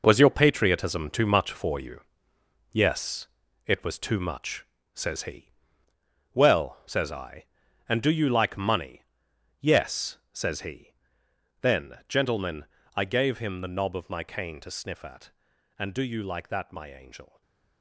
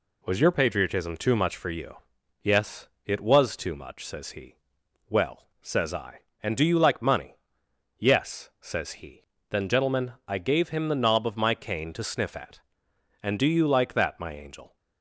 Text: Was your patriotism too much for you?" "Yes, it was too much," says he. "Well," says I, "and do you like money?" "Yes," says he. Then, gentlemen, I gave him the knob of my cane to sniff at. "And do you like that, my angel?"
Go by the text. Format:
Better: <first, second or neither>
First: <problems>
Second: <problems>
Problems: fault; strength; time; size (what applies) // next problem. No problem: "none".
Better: second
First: gets quieter; strong; throughout; 10 dB // stays silent after the last word; slight; from 17.2 s on; 0.6 s long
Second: none